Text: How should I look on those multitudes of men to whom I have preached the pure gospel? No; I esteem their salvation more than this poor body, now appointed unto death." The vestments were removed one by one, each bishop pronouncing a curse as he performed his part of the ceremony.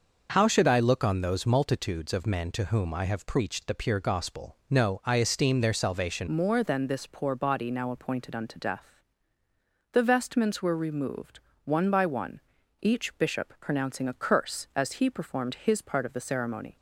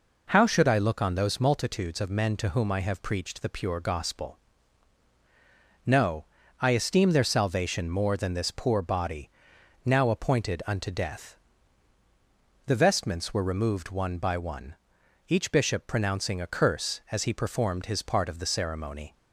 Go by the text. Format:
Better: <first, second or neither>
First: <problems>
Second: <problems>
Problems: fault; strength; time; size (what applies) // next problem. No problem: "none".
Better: second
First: changes voice at "more"; from 6.2 s on; 10.5 s long // pauses between "removed" and "one"; slight; at 11.3 s; 0.26 s long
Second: none